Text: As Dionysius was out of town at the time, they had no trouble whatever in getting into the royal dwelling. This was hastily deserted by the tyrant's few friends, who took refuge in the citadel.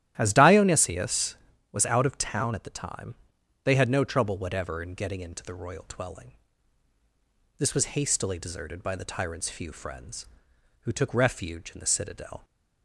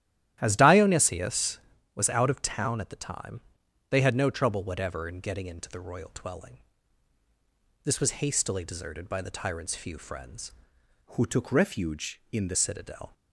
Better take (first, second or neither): first